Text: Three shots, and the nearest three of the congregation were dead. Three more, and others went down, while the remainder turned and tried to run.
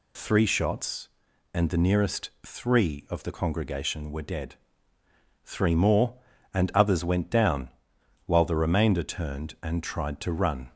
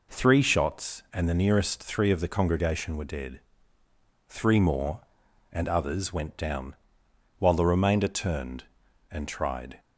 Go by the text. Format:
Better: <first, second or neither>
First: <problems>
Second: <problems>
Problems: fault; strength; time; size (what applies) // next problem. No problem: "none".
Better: first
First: none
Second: stops before "to run"; at 9.7 s